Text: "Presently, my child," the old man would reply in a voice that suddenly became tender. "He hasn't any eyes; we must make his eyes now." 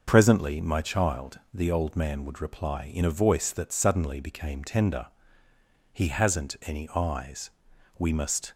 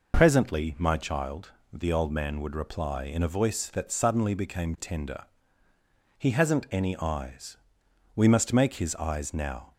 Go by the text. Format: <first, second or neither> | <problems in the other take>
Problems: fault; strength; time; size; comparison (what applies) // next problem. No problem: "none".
second | stops before "make his eyes now"; at 8.5 s